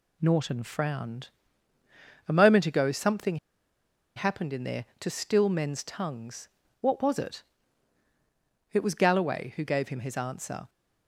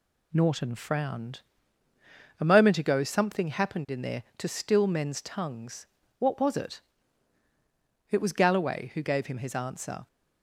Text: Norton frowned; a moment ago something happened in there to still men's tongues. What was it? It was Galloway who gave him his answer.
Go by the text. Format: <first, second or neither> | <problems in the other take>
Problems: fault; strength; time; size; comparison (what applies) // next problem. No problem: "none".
second | pauses between "something" and "happened"; noticeable; at 3.3 s; 0.80 s long